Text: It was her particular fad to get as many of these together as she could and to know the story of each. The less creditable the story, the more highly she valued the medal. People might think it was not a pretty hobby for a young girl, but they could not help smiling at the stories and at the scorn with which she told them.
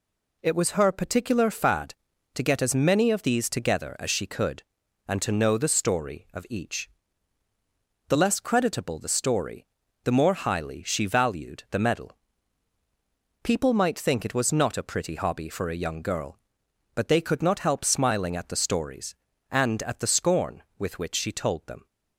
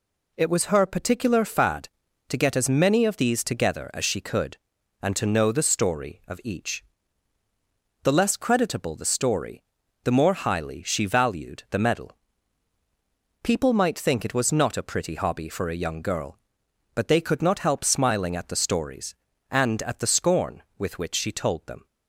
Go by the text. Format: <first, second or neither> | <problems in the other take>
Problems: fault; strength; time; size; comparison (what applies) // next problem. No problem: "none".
neither | none